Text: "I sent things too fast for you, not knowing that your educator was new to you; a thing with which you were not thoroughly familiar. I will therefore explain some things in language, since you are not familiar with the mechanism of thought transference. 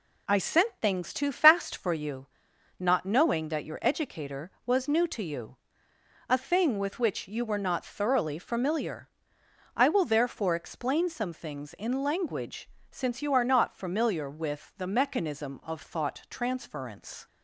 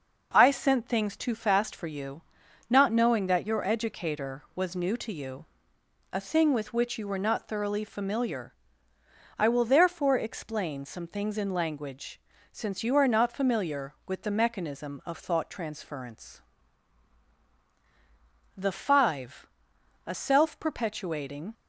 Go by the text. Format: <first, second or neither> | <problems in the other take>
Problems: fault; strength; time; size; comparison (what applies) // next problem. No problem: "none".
first | goes on to say "The Five a self perpetuating"; strong; from 18.5 s on; 2.9 s long